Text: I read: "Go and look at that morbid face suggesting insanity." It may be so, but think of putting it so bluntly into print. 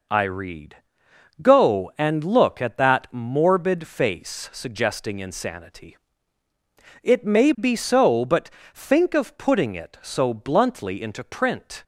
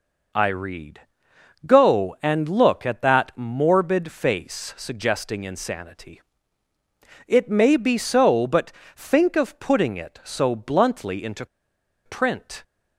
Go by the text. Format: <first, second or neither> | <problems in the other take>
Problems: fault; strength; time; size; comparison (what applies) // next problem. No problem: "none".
first | pauses between "but" and "think"; slight; at 8.7 s; 0.24 s long; slight in the first // pauses between "into" and "print"; noticeable; at 11.4 s; 0.58 s long